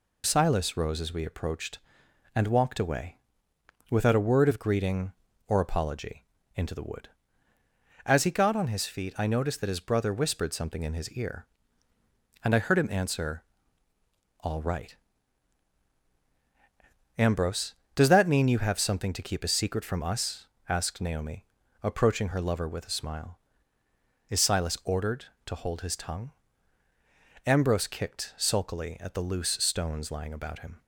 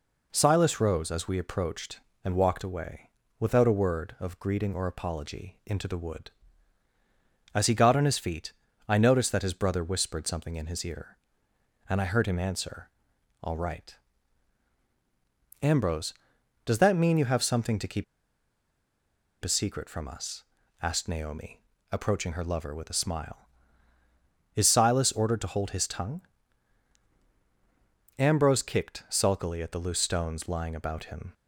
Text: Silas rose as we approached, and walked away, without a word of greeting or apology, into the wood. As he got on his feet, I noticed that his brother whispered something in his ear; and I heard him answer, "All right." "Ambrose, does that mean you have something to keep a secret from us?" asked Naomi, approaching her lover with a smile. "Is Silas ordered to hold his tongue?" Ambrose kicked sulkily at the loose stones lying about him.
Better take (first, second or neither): first